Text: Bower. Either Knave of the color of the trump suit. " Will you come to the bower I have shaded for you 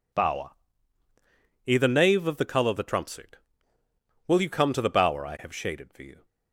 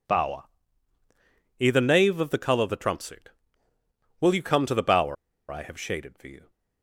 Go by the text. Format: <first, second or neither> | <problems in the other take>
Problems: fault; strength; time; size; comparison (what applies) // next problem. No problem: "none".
first | pauses between "bower" and "I"; at 5.1 s; 0.36 s long